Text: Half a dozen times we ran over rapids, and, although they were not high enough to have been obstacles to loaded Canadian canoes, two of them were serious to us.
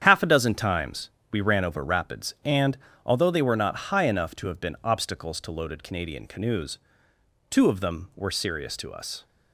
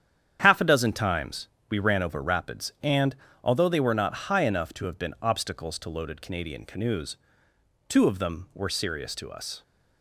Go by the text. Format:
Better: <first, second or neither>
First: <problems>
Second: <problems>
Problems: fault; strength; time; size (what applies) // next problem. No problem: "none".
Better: neither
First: starts louder than the rest; strong; until 1.0 s; 9 dB // pauses between "times" and "we"; slight; at 1.1 s; 0.20 s long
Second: starts louder than the rest; strong; until 1.4 s; 9 dB // pauses between "times" and "we"; slight; at 1.4 s; 0.20 s long